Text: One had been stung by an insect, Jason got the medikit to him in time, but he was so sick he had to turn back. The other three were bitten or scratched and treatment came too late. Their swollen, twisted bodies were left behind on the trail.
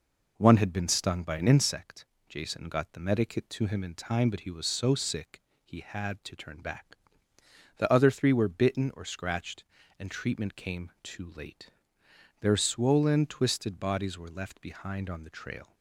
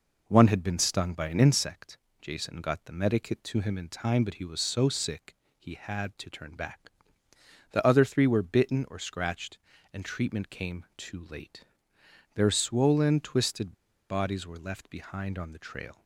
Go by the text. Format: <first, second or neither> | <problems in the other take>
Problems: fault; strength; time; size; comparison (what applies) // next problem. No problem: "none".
first | pauses between "sick" and "he"; slight; at 5.3 s; 0.20 s long; slight in the first // pauses between "twisted" and "bodies"; at 13.7 s; 0.37 s long